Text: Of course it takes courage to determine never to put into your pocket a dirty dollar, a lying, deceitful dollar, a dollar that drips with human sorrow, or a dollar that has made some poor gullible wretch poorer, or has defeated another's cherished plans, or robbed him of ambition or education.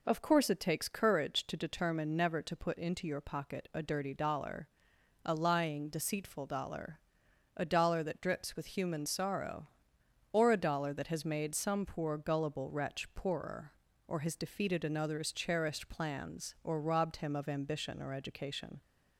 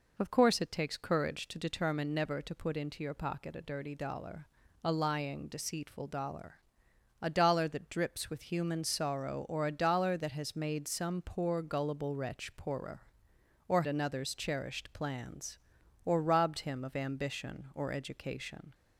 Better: first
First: none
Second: skips "has defeated"; at 13.8 s

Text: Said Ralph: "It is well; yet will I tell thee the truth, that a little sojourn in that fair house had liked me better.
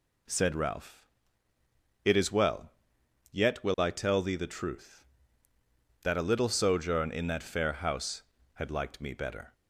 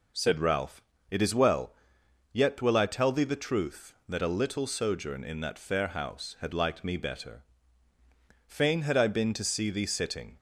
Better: first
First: none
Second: goes on to say "Fain had I been to see thee sitting"; strong; from 8.4 s on; 1.9 s long

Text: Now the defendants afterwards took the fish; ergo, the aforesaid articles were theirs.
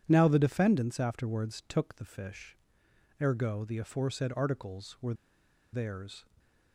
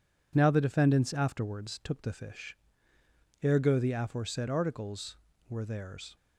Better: second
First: pauses between "were" and "theirs"; noticeable; at 5.1 s; 0.58 s long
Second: none

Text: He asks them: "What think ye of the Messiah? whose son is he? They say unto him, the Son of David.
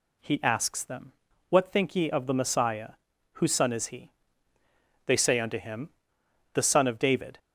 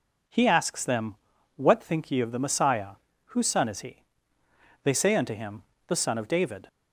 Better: neither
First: none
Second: none

